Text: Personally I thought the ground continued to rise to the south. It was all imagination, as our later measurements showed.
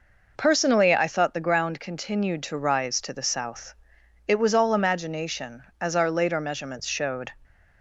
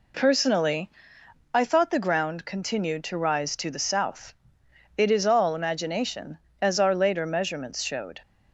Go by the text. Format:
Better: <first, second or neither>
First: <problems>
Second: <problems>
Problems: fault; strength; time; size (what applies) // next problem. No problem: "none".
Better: first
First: none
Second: pauses between "Personally" and "I"; noticeable; at 0.8 s; 0.64 s long // says "is" for "was"; at 5.1 s